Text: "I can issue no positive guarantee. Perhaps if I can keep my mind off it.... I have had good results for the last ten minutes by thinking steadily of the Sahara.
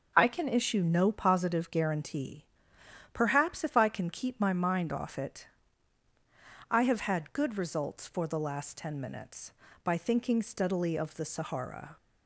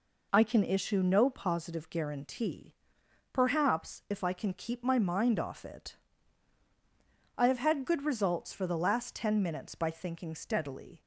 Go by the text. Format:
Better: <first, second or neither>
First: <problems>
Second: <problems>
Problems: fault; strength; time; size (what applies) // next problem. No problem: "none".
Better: first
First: none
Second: stops before "of the Sahara"; at 11.0 s